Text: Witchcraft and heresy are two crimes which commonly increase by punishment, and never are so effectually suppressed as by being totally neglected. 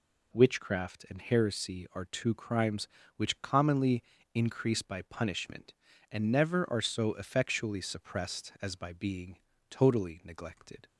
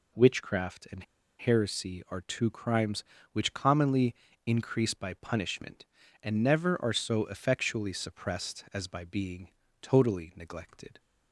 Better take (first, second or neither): first